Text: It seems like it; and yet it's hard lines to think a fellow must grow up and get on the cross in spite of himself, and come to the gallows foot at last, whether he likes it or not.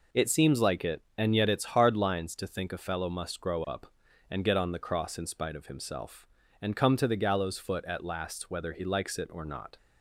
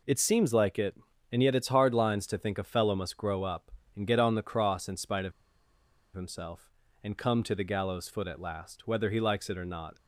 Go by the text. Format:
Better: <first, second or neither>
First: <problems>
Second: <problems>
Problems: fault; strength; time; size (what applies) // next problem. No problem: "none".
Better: first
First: none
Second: pauses between "of" and "himself"; noticeable; at 5.3 s; 0.82 s long